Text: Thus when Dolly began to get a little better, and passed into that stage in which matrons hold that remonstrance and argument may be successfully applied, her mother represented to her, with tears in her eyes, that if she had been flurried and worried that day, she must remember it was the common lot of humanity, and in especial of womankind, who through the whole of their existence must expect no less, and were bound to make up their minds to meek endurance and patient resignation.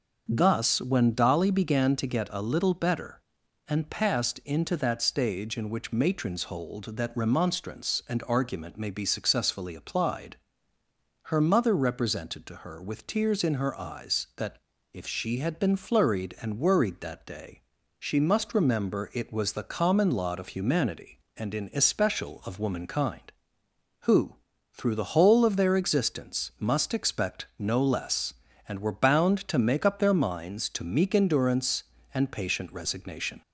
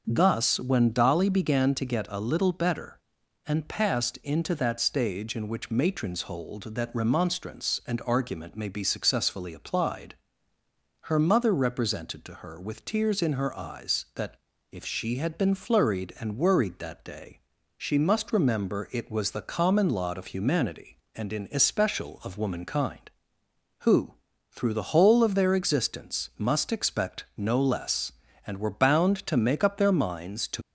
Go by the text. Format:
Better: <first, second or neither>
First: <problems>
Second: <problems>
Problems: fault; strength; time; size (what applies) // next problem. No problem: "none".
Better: first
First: pauses between "that" and "if"; slight; at 14.5 s; 0.36 s long // pauses between "who" and "through"; at 24.3 s; 0.38 s long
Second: pauses between "that" and "if"; slight; at 14.3 s; 0.36 s long // pauses between "who" and "through"; at 24.1 s; 0.38 s long // stops before "meek endurance and patient resignation"; at 30.6 s